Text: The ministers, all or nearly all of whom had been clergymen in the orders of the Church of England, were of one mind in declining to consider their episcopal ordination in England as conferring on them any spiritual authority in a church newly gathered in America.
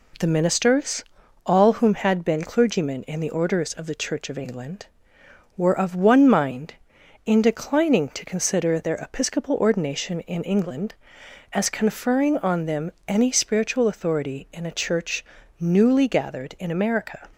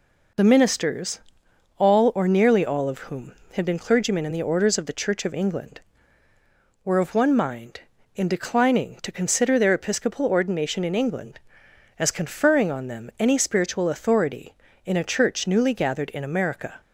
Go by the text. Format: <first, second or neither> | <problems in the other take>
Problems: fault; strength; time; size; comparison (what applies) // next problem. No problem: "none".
second | skips "or nearly all of"; at 1.7 s // pauses between "them" and "any"; slight; at 12.9 s; 0.16 s long // pauses between "church" and "newly"; slight; at 15.2 s; 0.34 s long